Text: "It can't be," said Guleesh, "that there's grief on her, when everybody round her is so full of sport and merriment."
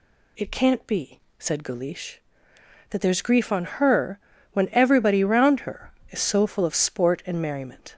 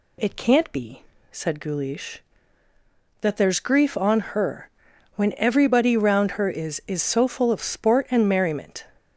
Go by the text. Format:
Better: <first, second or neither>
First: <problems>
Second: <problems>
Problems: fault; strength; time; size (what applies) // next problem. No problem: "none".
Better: first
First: none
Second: says "is" twice; at 6.8 s